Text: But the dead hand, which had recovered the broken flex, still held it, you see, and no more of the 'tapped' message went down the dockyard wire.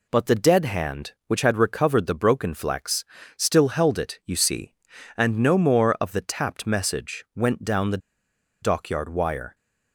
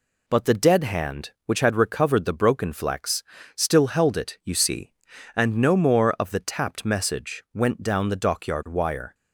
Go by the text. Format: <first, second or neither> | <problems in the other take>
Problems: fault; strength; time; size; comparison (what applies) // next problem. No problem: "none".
second | pauses between "the" and "dockyard"; noticeable; at 7.9 s; 0.64 s long